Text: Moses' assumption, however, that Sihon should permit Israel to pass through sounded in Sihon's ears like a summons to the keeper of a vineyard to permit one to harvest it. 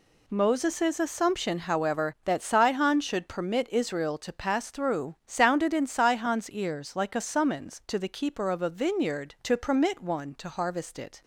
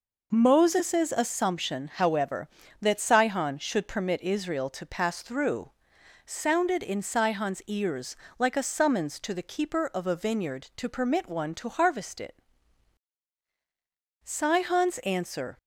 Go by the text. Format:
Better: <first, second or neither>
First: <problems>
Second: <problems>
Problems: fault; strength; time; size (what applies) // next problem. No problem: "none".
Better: first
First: none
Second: pauses between "through" and "sounded"; noticeable; at 5.7 s; 0.52 s long // pauses between "ears" and "like"; slight; at 8.1 s; 0.24 s long // goes on to say "Sihon's answer"; from 14.2 s on; 1.3 s long